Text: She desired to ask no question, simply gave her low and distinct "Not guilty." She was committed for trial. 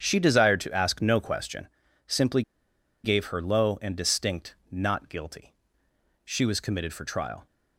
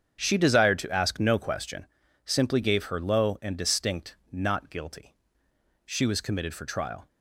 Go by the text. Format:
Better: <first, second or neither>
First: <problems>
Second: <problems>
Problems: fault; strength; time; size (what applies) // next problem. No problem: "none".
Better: second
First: starts louder than the rest; strong; until 1.0 s; 8 dB // pauses between "simply" and "gave"; noticeable; at 2.4 s; 0.62 s long // pauses between "distinct" and "Not"; slight; at 4.5 s; 0.16 s long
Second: starts louder than the rest; strong; until 1.2 s; 8 dB // pauses between "distinct" and "Not"; slight; at 4.1 s; 0.16 s long